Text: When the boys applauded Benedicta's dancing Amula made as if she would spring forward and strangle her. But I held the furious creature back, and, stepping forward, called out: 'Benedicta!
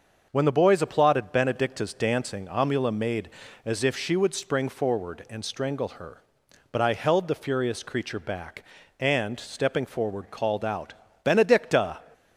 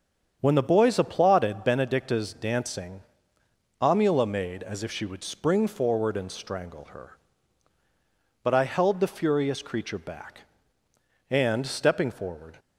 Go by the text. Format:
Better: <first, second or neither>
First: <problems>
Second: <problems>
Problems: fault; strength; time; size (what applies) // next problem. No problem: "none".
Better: first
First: starts louder than the rest; until 1.3 s; 6.5 dB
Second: starts louder than the rest; strong; until 1.4 s; 7.5 dB // pauses between "dancing" and "Amula"; noticeable; at 3.0 s; 0.78 s long // stops before "called out Benedicta"; at 12.5 s